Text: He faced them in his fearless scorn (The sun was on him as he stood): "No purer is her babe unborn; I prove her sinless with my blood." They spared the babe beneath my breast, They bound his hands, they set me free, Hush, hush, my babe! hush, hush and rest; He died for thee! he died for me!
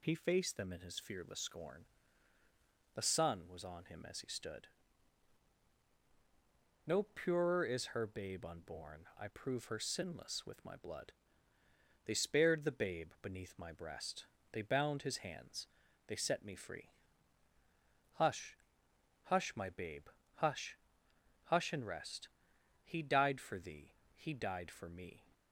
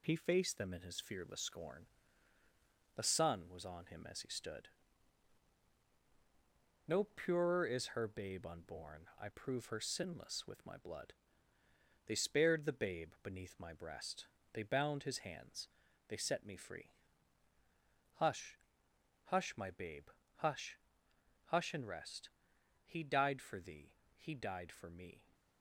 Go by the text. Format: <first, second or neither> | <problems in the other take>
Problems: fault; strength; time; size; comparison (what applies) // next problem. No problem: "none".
first | gets quieter; throughout; 4 dB